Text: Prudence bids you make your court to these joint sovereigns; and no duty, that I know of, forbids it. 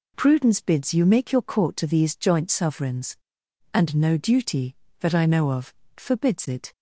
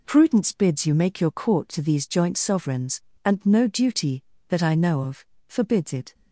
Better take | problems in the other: neither | none

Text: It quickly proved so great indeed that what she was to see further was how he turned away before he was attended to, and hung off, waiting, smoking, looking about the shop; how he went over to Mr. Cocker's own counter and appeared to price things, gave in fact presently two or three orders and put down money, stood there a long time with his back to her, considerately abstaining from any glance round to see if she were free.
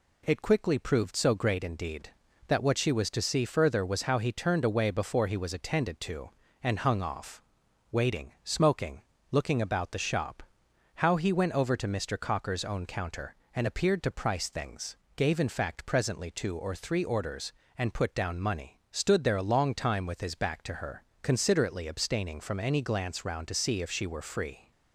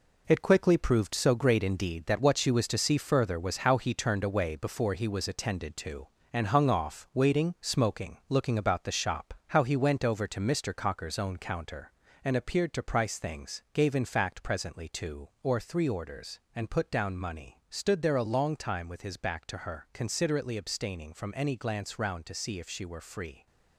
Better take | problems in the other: first | gets quieter; strong; throughout; 8 dB

